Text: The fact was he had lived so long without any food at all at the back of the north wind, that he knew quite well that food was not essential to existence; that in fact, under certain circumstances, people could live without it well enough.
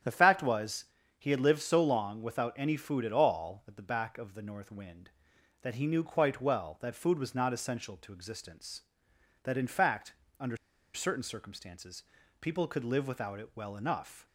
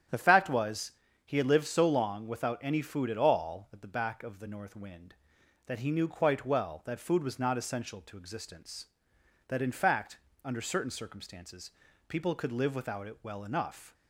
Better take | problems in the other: second | starts louder than the rest; strong; until 1.3 s; 9.5 dB; strong in the second // pauses between "was" and "he"; slight; at 0.8 s; 0.32 s long; slight in the second // pauses between "under" and "certain"; at 10.5 s; 0.37 s long

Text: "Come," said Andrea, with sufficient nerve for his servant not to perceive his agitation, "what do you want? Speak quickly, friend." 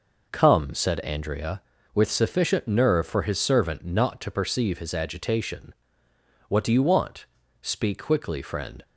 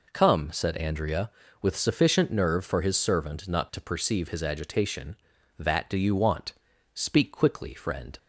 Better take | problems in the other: first | says "that" for "what"; at 5.5 s

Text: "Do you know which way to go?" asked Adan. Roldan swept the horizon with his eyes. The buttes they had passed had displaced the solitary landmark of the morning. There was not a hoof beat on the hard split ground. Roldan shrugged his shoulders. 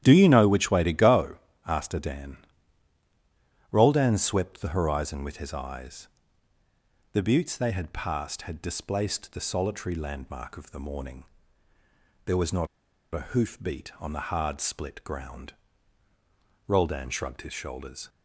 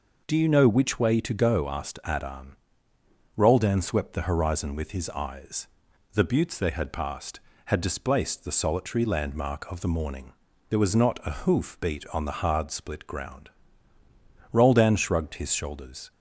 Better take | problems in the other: second | starts louder than the rest; strong; until 1.0 s; 11 dB // pauses between "not" and "a"; at 12.6 s; 0.45 s long

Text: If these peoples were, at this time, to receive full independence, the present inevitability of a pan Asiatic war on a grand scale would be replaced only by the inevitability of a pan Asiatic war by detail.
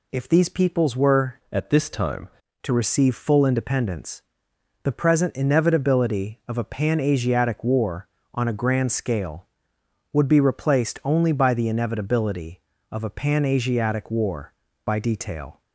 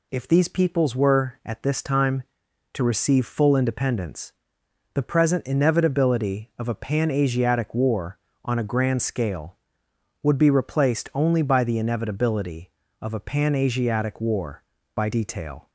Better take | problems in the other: second | changes voice from "at" to "time"; from 1.5 to 2.2 s; 0.7 s long

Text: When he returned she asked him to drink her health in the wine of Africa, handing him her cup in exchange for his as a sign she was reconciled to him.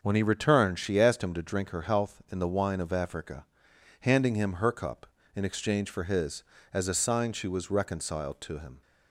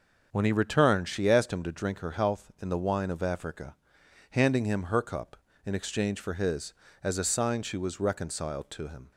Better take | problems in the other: neither | starts louder than the rest; the same in both

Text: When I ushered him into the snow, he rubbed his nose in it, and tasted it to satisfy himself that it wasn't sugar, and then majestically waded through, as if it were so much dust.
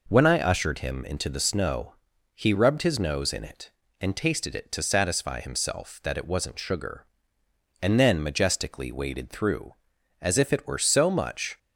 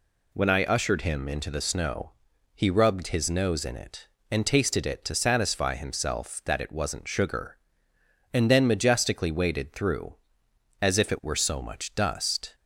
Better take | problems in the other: second | stops before "dust"; at 11.5 s

